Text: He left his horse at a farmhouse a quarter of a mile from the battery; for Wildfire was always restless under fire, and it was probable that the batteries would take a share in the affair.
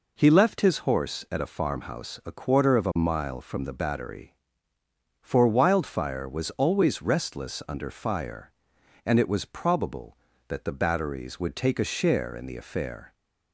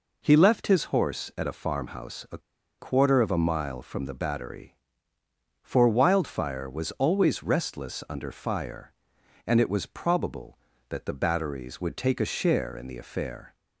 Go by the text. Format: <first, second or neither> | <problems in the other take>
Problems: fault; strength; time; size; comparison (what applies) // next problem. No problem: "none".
first | pauses between "a" and "quarter"; at 2.3 s; 0.41 s long